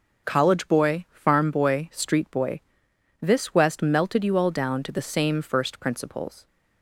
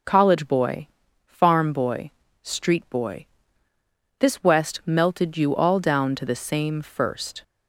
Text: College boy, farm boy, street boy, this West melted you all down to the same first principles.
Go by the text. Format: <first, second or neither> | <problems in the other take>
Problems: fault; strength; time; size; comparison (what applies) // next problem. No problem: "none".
first | stops before "principles"; at 7.4 s